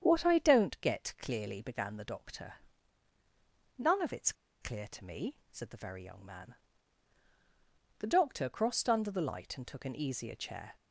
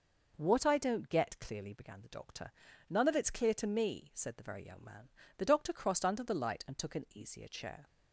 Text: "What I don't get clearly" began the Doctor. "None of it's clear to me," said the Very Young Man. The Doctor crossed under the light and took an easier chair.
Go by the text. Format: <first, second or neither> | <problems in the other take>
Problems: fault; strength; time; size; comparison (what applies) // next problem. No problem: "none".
second | starts louder than the rest; strong; until 1.0 s; 8 dB // pauses between "it's" and "clear"; slight; at 4.3 s; 0.28 s long